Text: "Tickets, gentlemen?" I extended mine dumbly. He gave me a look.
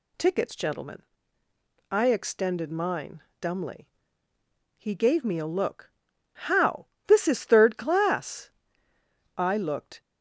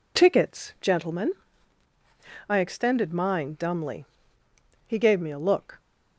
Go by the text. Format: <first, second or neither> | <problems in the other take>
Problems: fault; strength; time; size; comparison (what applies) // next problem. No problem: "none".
second | pauses between "mine" and "dumbly"; slight; at 3.2 s; 0.20 s long // goes on to say "How This is third class I looked"; strong; from 6.3 s on; 3.7 s long